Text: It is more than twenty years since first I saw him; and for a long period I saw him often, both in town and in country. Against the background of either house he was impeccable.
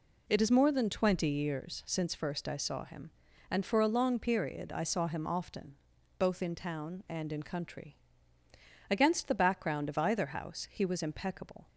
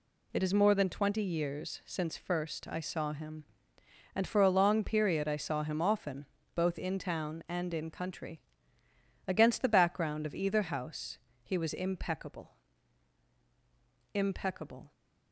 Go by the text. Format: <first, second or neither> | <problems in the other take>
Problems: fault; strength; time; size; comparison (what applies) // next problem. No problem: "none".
first | pauses between "house" and "he"; slight; at 11.1 s; 0.26 s long // says "impeccable" twice; at 14.1 s